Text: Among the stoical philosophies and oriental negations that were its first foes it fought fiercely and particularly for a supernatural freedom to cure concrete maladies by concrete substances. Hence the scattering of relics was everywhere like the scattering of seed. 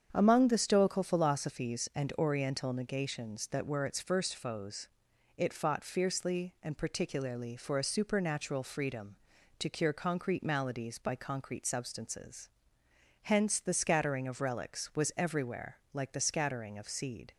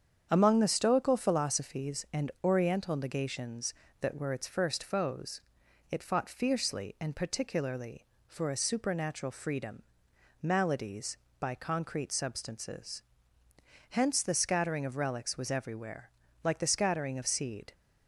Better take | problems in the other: first | starts louder than the rest; strong; until 1.3 s; 8 dB; strong in the first // pauses between "foes" and "it"; noticeable; at 5.4 s; 0.48 s long; noticeable in the first // skips "to cure concrete"; at 10.1 s // pauses between "everywhere" and "like"; slight; at 16.0 s; 0.32 s long; slight in the first

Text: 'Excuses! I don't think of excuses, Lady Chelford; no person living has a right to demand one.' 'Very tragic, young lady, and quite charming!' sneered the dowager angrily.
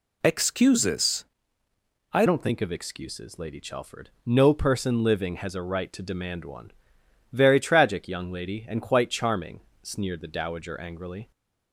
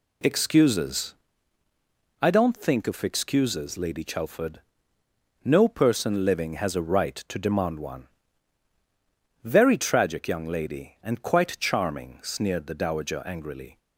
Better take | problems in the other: second | changes voice at "don't"; from 2.2 s on; 9.1 s long

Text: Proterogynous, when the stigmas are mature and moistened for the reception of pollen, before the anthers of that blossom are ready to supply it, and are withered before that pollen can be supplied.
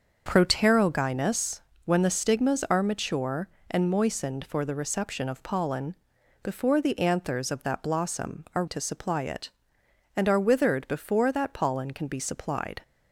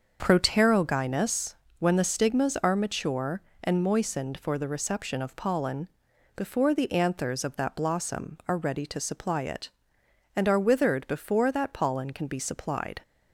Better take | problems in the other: second | starts louder than the rest; until 1.2 s; 6.5 dB; also in the second // skips "ready"; at 8.6 s

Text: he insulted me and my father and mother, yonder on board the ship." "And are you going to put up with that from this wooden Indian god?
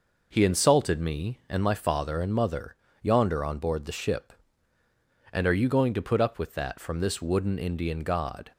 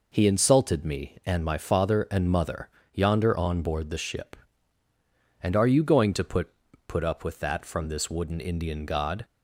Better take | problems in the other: first | says "put" twice; at 6.8 s

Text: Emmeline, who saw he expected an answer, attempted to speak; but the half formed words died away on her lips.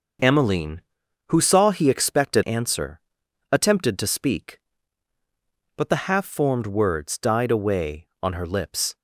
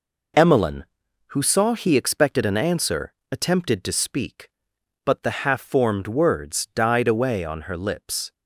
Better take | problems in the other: second | skips "an"; at 2.4 s

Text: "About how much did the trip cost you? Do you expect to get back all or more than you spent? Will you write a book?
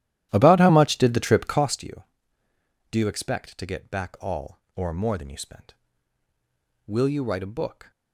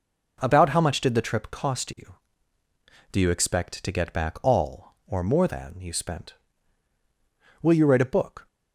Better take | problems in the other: second | starts louder than the rest; strong; until 1.9 s; 12.5 dB

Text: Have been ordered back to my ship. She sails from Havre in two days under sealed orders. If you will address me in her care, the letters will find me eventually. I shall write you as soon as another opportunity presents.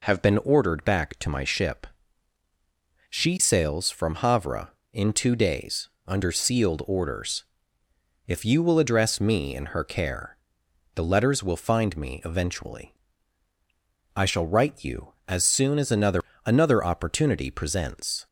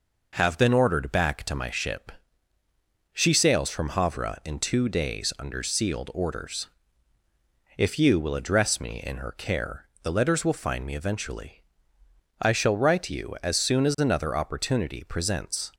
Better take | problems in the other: second | pauses between "days" and "under"; slight; at 5.8 s; 0.18 s long // says "another" twice; at 16.4 s

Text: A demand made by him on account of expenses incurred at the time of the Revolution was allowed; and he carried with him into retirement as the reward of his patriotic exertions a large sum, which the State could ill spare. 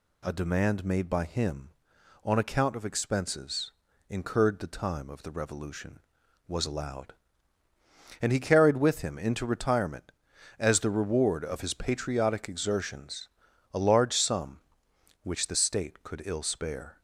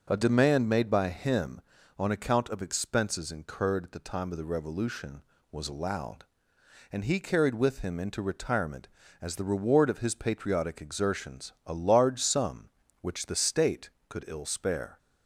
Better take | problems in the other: second | pauses between "expenses" and "incurred"; slight; at 3.7 s; 0.36 s long // skips "at"; at 4.5 s // pauses between "exertions" and "a"; at 13.2 s; 0.44 s long

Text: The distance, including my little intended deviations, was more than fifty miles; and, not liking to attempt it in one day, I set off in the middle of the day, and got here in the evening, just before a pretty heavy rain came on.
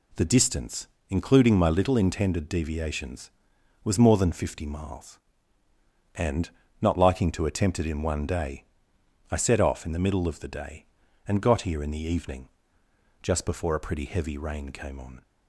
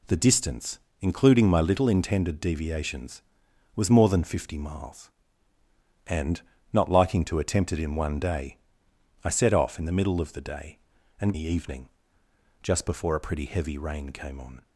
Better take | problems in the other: first | skips "got here in"; at 11.3 s

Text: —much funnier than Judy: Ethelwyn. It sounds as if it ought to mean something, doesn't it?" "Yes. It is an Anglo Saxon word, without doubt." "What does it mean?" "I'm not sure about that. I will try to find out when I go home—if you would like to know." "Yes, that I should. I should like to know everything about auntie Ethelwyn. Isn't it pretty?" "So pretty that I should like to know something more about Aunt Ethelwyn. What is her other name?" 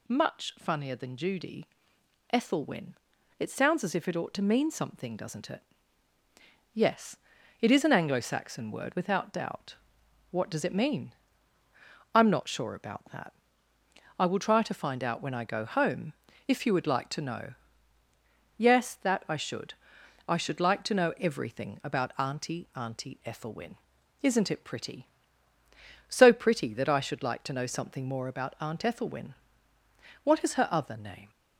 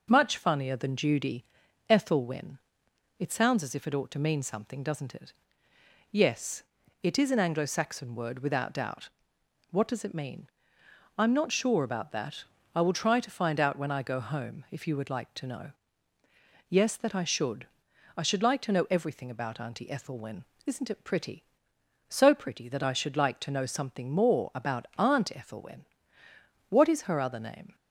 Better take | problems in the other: second | says "auntie" twice; at 22.7 s

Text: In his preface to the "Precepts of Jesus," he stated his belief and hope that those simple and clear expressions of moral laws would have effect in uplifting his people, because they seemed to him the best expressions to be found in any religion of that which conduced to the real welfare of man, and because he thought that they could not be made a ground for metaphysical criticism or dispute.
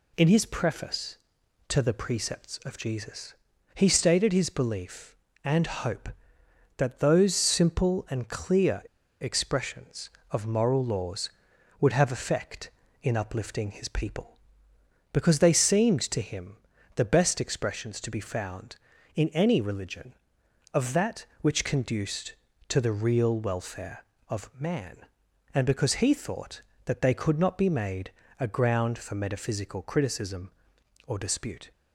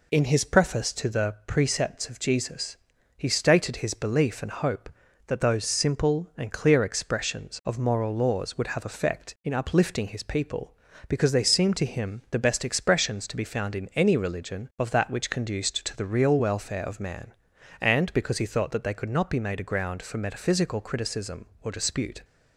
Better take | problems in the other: second | pauses between "clear" and "expressions"; at 8.8 s; 0.39 s long // pauses between "him" and "the"; at 16.5 s; 0.40 s long // pauses between "made" and "a"; slight; at 28.1 s; 0.28 s long

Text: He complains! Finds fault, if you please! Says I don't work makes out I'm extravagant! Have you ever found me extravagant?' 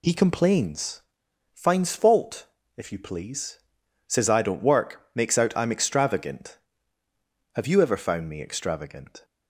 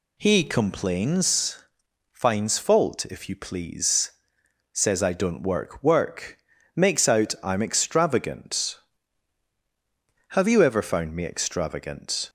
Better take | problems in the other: first | says "work" twice; at 5.8 s

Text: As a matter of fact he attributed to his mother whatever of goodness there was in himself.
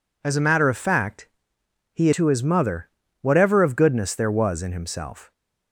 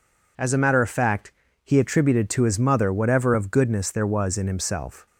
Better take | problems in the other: second | pauses between "fact" and "he"; noticeable; at 1.2 s; 0.66 s long; slight in the second // skips "attributed"; at 2.1 s // pauses between "mother" and "whatever"; slight; at 2.8 s; 0.32 s long

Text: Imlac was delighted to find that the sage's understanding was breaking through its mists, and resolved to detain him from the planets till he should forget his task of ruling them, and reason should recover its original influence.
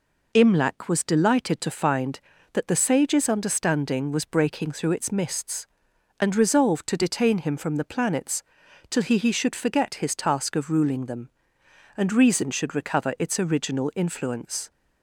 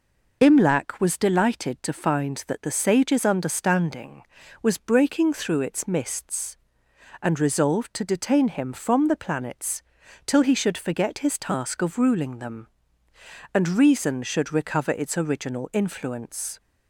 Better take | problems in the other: second | pauses between "planets" and "till"; noticeable; at 8.4 s; 0.48 s long; also in the second // says "he" twice; at 9.1 s

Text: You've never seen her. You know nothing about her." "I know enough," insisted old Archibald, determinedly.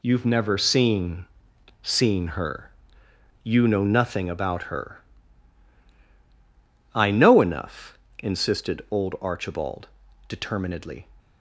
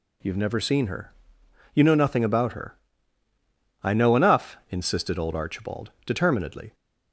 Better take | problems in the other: second | says "seen" twice; at 1.8 s

